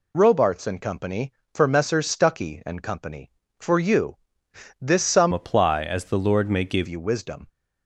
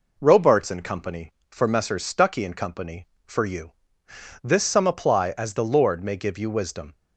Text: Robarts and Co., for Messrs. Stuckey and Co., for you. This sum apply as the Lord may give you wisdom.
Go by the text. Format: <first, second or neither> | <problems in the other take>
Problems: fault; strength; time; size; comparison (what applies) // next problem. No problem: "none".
second | changes voice from "apply" to "give"; from 5.3 to 6.8 s; 1.5 s long